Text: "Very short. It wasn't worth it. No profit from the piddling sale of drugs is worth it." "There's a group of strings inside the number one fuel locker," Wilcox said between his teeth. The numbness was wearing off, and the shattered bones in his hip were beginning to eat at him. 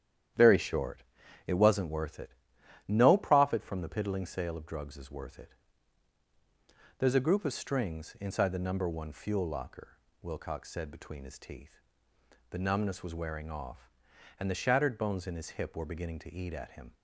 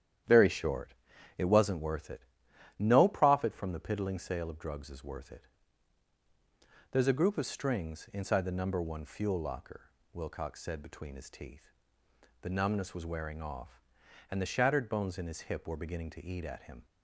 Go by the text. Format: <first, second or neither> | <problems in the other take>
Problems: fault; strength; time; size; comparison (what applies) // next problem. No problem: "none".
neither | starts louder than the rest; strong; the same in both